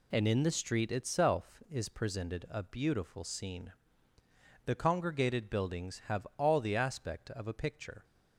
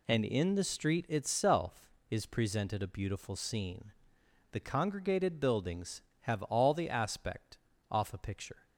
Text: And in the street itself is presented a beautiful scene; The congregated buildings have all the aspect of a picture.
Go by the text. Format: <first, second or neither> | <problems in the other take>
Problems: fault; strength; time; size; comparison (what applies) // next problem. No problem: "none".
first | says "off" for "of"; at 7.9 s